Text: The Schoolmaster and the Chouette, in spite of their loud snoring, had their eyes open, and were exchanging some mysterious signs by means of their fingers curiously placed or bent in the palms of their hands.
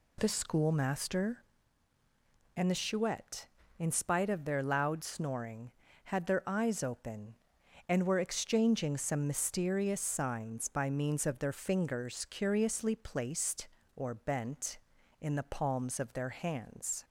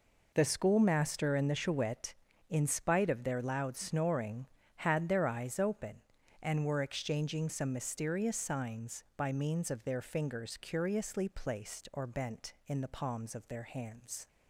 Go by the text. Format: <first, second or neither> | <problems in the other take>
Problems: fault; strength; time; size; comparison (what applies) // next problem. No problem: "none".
neither | none